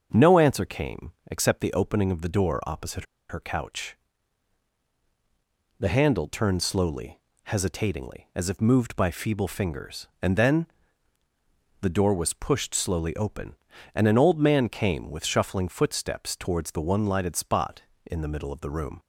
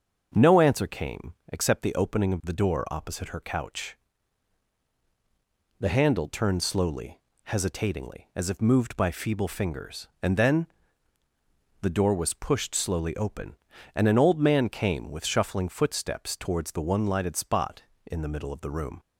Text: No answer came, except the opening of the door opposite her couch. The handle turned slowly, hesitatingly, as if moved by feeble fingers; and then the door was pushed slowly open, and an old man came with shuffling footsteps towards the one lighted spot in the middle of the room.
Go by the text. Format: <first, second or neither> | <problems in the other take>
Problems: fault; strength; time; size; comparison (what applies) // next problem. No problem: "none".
second | starts louder than the rest; until 1.3 s; 6.5 dB; also in the second // pauses between "opposite" and "her"; slight; at 3.0 s; 0.24 s long // pauses between "then" and "the"; at 10.6 s; 1.1 s long; also in the second